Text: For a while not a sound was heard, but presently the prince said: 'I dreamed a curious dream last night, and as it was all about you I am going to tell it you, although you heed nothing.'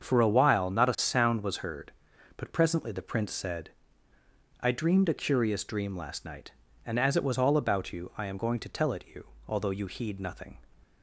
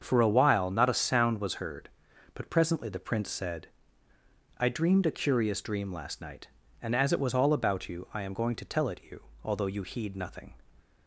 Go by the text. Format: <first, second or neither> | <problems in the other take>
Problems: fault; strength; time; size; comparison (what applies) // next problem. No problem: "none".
neither | starts louder than the rest; the same in both